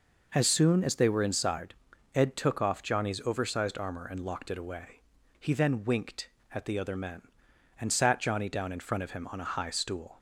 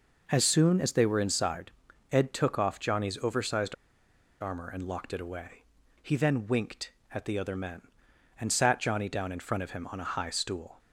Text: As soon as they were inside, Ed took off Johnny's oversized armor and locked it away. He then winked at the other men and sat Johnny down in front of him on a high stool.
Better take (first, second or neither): first